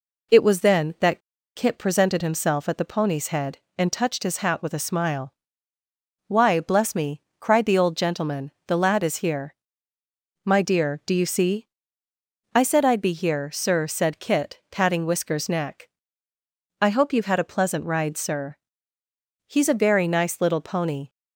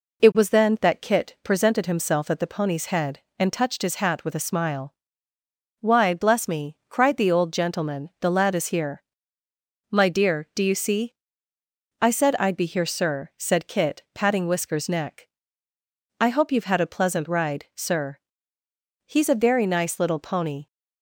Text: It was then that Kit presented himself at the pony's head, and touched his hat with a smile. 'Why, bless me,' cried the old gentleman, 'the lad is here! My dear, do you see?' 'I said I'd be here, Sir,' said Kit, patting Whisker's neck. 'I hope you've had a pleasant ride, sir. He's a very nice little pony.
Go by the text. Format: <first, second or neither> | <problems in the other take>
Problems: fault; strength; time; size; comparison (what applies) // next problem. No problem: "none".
second | pauses between "that" and "Kit"; slight; at 1.2 s; 0.35 s long